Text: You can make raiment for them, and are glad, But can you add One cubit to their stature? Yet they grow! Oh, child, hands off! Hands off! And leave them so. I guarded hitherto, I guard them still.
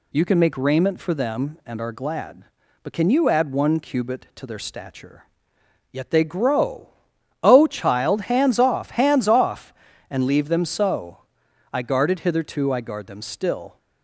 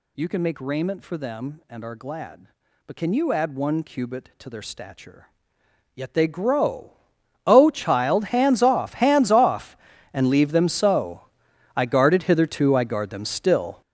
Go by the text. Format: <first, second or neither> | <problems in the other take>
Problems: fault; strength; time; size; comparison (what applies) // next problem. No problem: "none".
first | gets louder; strong; throughout; 11 dB